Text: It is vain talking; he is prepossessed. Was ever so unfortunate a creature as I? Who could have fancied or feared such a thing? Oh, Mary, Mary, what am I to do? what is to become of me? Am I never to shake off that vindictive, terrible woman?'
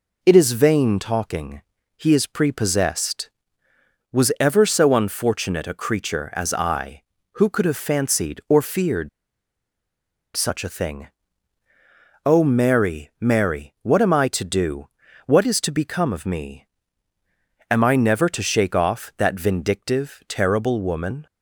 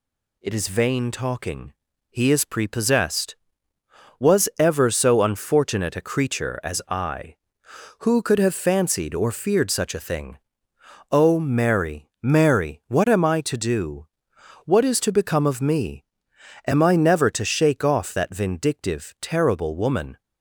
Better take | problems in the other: second | pauses between "feared" and "such"; strong; at 9.0 s; 1.2 s long

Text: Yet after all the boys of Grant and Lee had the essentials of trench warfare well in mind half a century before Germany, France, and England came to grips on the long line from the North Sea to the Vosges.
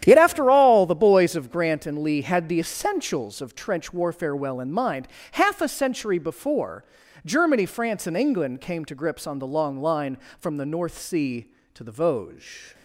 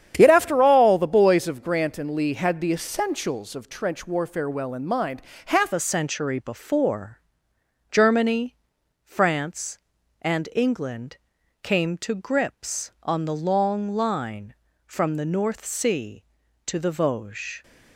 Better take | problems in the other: first | starts louder than the rest; strong; until 1.1 s; 9 dB; strong in the first // pauses between "mind" and "half"; slight; at 5.2 s; 0.24 s long; slight in the first // changes voice at "a"; from 5.7 s on; 11.9 s long // pauses between "before" and "Germany"; noticeable; at 7.2 s; 0.70 s long; also in the first // pauses between "England" and "came"; noticeable; at 11.1 s; 0.46 s long

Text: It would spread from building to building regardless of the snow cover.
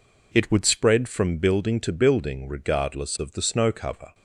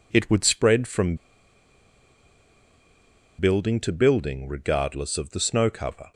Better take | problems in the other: first | pauses between "from" and "building"; strong; at 1.1 s; 2.2 s long

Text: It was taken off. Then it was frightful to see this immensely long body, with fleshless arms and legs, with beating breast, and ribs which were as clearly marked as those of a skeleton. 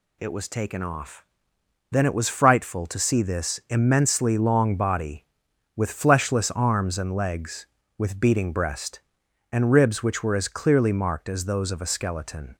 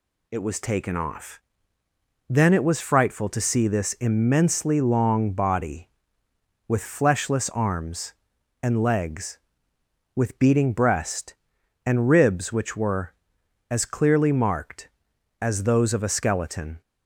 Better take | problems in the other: neither | none

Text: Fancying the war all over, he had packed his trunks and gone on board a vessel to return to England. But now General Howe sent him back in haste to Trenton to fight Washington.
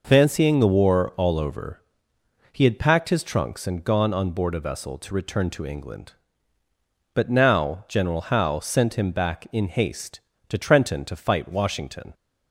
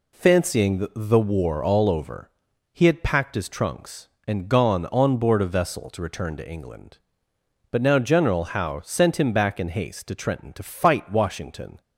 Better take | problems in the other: first | says "the" twice; at 0.9 s

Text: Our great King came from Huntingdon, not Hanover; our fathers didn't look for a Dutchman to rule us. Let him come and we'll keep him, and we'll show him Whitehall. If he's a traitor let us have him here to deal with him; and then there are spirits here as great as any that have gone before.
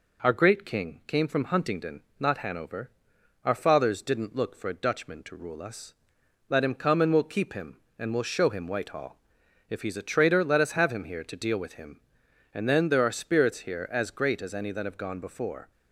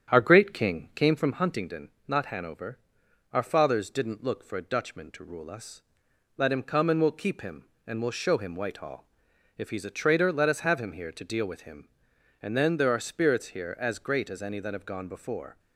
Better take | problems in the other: first | starts louder than the rest; strong; until 1.4 s; 8.5 dB

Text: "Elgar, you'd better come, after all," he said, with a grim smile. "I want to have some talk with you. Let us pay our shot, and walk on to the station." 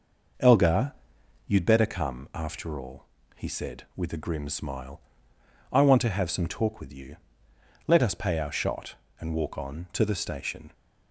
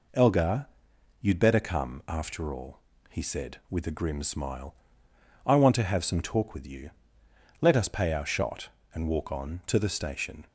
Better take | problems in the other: second | starts louder than the rest; noticeable; until 1.7 s; 5.5 dB

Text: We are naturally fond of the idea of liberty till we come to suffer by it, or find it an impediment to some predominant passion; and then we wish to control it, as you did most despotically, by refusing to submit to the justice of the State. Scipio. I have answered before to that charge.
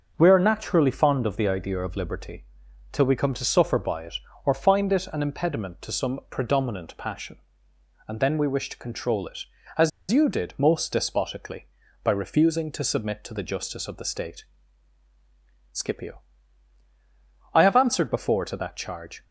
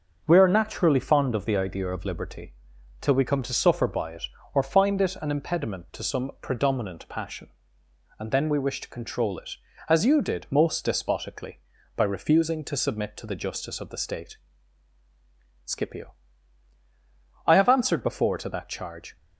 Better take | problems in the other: second | starts louder than the rest; noticeable; until 1.1 s; 6 dB; noticeable in the second // pauses between "liberty" and "till"; noticeable; at 2.4 s; 0.48 s long; noticeable in the second // pauses between "as" and "you"; slight; at 9.9 s; 0.21 s long

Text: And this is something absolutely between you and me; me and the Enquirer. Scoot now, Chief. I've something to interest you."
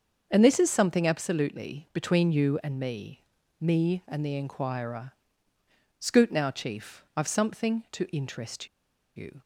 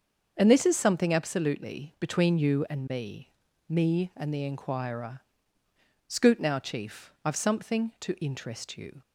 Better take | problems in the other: second | starts louder than the rest; until 1.3 s; 6.5 dB; also in the second // pauses between "interest" and "you"; noticeable; at 8.6 s; 0.48 s long

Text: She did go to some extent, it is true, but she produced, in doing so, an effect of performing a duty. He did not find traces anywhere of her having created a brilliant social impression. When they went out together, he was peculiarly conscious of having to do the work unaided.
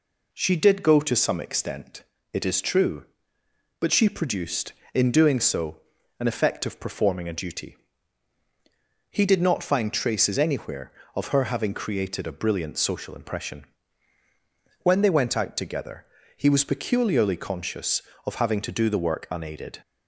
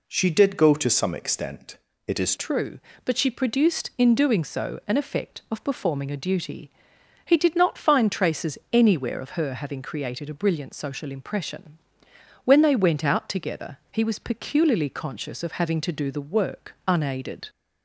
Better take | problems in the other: first | changes voice at "true"; from 2.3 s on; 15.1 s long // pauses between "traces" and "anywhere"; slight; at 8.5 s; 0.16 s long

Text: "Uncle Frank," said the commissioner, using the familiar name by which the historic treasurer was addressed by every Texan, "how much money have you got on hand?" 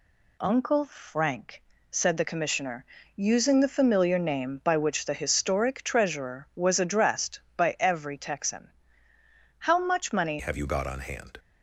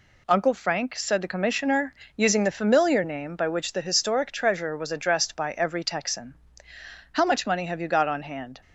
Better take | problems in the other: second | changes voice at "have"; from 10.3 s on; 1.0 s long

